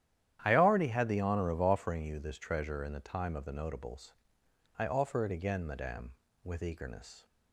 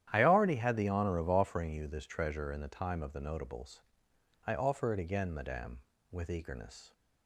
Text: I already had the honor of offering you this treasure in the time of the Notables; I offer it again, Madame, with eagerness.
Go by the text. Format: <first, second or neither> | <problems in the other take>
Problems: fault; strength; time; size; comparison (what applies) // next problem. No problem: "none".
neither | starts louder than the rest; strong; the same in both